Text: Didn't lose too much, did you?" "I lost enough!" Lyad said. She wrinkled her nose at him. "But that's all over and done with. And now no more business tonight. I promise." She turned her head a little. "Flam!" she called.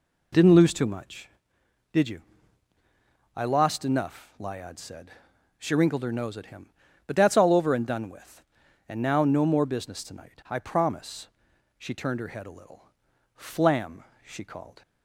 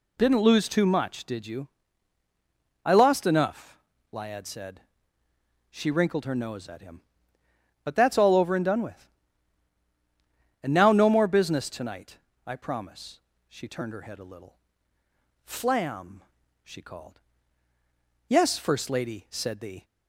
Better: first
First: none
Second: goes on to say "Yes First Lady said the"; from 18.2 s on; 1.5 s long

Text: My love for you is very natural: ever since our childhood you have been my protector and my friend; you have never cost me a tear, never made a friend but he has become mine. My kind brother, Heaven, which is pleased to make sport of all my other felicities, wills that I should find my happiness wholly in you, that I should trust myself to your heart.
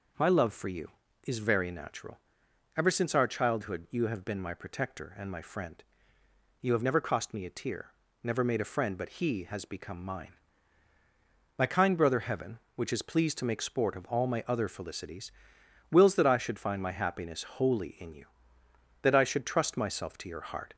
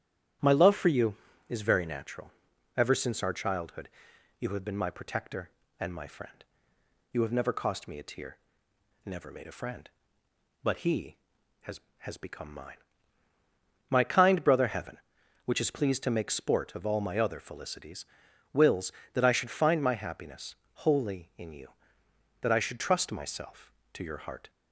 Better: first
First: none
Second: starts louder than the rest; strong; until 1.7 s; 10.5 dB // pauses between "childhood" and "you"; noticeable; at 3.8 s; 0.50 s long // says "has" twice; at 12.0 s // pauses between "happiness" and "wholly"; slight; at 20.5 s; 0.30 s long

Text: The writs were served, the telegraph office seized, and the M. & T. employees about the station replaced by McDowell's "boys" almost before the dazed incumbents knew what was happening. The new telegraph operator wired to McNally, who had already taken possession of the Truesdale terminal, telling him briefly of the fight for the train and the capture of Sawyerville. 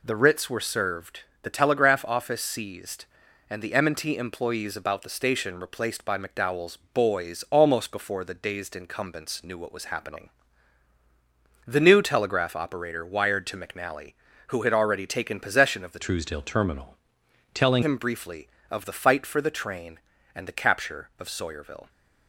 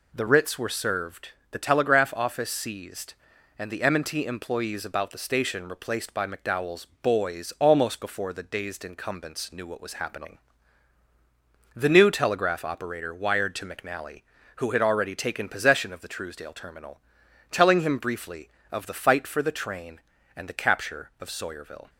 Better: second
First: pauses between "McDowell's" and "boys"; slight; at 6.7 s; 0.16 s long // changes voice from "Truesdale" to "telling"; from 15.9 to 17.8 s; 1.9 s long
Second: pauses between "McDowell's" and "boys"; slight; at 6.8 s; 0.16 s long

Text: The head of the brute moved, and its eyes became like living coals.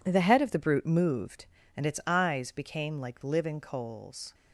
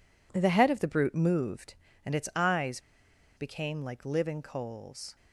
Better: first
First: none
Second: pauses between "eyes" and "became"; noticeable; at 2.7 s; 0.57 s long

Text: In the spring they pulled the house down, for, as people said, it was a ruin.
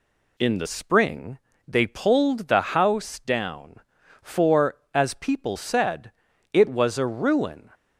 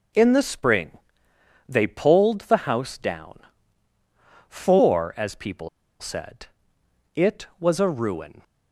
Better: first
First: pauses between "spring" and "they"; slight; at 1.3 s; 0.28 s long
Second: starts louder than the rest; until 1.9 s; 6 dB // pauses between "spring" and "they"; noticeable; at 0.9 s; 0.76 s long // pauses between "people" and "said"; slight; at 5.6 s; 0.32 s long

